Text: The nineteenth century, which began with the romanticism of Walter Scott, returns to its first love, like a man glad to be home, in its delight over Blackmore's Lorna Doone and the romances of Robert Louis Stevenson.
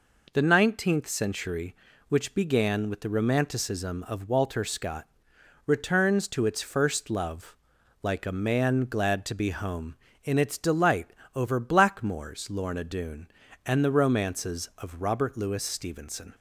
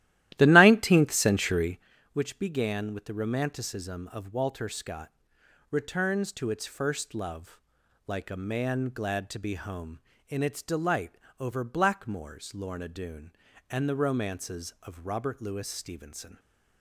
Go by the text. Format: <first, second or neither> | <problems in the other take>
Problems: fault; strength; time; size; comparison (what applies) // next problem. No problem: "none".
first | starts louder than the rest; strong; until 1.9 s; 14.5 dB // pauses between "delight" and "over"; slight; at 11.1 s; 0.28 s long; slight in the first